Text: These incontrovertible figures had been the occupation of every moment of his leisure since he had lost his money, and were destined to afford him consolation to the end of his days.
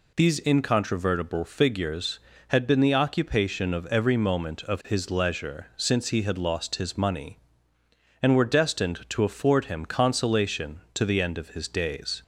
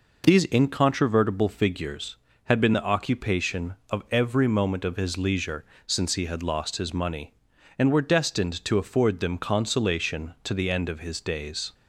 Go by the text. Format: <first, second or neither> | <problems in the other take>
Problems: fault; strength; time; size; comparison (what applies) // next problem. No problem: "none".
first | pauses between "leisure" and "since"; slight; at 5.6 s; 0.20 s long // says "them" for "him"; at 9.1 s